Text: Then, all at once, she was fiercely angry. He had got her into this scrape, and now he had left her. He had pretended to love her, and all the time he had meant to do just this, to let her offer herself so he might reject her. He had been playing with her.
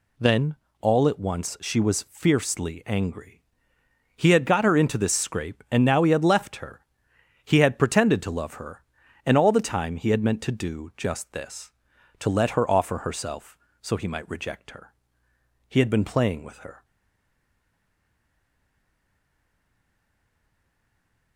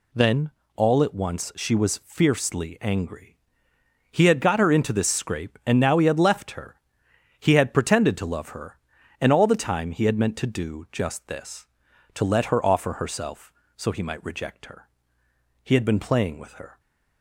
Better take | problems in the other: second | stays silent after the last word; strong; from 16.8 s on; 4.5 s long

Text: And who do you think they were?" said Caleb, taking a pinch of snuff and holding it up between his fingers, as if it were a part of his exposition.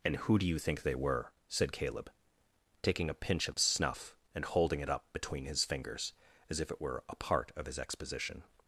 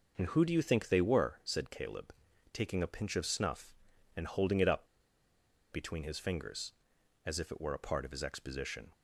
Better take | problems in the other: first | pauses between "up" and "between"; noticeable; at 4.8 s; 0.87 s long

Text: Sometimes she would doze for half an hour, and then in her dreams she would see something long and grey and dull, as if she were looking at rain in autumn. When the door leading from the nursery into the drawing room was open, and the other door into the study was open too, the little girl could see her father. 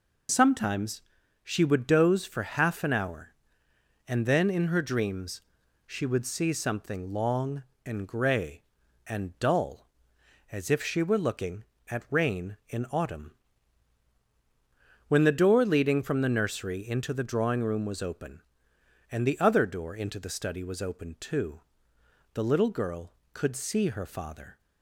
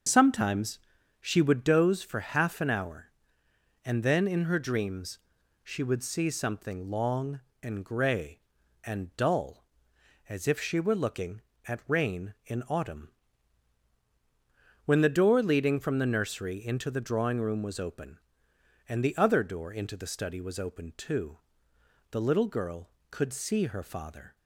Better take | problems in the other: first | starts louder than the rest; until 1.7 s; 6.5 dB // pauses between "Sometimes" and "she"; at 0.7 s; 0.40 s long; also in the first // pauses between "dreams" and "she"; noticeable; at 5.1 s; 0.46 s long; noticeable in the first

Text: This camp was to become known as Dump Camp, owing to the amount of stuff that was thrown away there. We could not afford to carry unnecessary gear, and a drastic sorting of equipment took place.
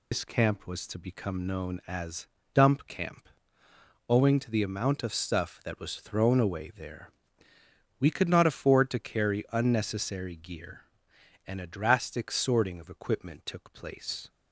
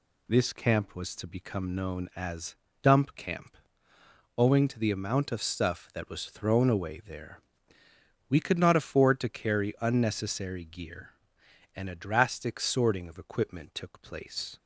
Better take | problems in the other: second | loses the start of "This"; at 0.1 s; 115 ms // pauses between "as" and "Dump"; slight; at 2.2 s; 0.26 s long; slight in the second

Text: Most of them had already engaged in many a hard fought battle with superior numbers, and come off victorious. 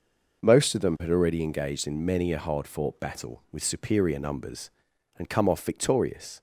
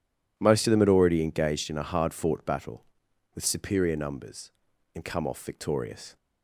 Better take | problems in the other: first | skips "many"; at 1.7 s

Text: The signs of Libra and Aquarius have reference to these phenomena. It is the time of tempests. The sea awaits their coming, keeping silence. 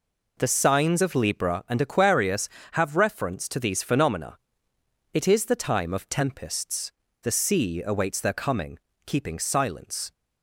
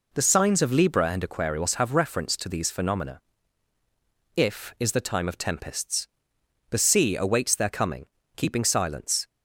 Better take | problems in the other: first | says "If" for "It"; at 4.3 s

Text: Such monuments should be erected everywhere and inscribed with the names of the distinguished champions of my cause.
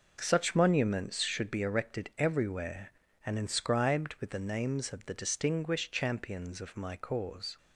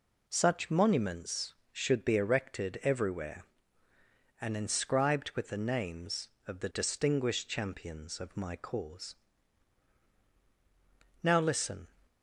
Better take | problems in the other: first | goes on to say "Now listen"; noticeable; from 11.2 s on; 0.66 s long

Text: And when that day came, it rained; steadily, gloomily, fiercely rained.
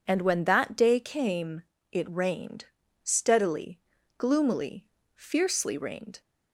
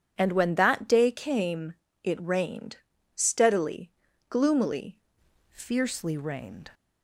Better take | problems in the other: first | changes voice at "fiercely"; from 5.5 s on; 1.2 s long

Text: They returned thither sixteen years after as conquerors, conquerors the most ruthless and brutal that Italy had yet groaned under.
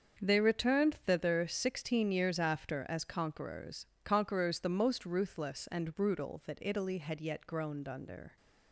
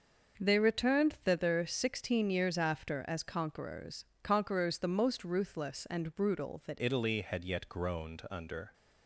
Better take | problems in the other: first | starts louder than the rest; until 1.4 s; 6.5 dB; strong in the first // changes voice at "Italy"; from 6.7 s on; 2.0 s long

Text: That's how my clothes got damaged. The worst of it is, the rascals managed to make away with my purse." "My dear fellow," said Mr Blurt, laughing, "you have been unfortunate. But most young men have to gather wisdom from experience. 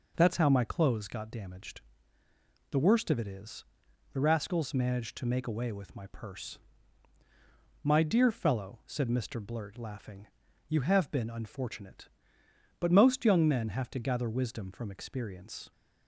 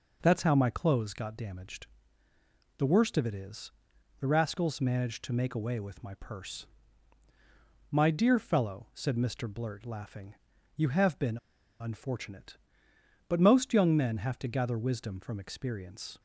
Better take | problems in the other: first | pauses between "been" and "unfortunate"; at 11.3 s; 0.41 s long

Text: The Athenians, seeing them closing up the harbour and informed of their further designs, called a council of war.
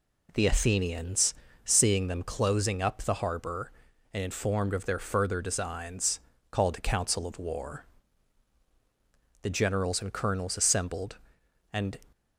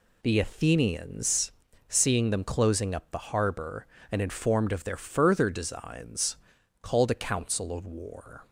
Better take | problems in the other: second | goes on to say "The generals and colonels assembled and"; strong; from 9.4 s on; 2.5 s long

